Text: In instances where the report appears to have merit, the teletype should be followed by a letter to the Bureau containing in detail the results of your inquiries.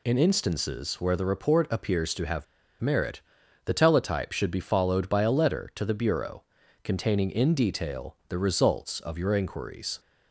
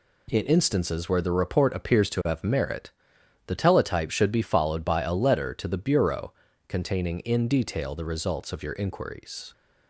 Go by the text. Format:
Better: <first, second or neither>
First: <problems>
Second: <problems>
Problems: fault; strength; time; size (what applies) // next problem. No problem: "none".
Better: second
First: pauses between "have" and "merit"; at 2.4 s; 0.36 s long // pauses between "Bureau" and "containing"; at 6.4 s; 0.40 s long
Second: pauses between "Bureau" and "containing"; slight; at 6.3 s; 0.36 s long